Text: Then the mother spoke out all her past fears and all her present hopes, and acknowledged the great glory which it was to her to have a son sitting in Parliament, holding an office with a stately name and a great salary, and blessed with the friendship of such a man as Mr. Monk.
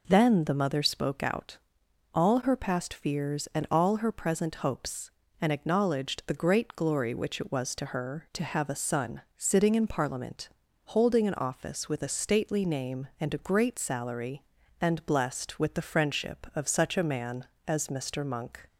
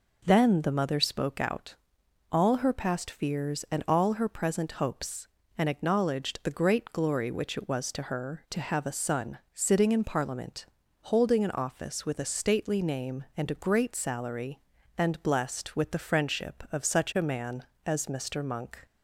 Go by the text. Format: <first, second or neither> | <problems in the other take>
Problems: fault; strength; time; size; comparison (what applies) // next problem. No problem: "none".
neither | pauses between "out" and "all"; noticeable; the same in both // pauses between "son" and "sitting"; slight; the same in both